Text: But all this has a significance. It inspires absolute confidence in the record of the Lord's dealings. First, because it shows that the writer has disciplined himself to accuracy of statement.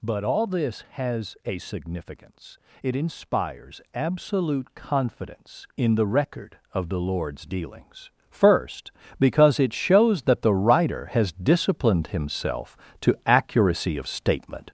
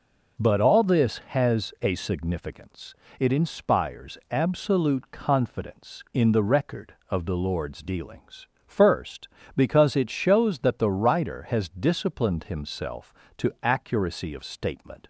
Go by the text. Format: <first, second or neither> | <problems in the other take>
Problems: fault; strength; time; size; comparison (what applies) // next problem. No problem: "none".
second | gets louder; noticeable; throughout; 5 dB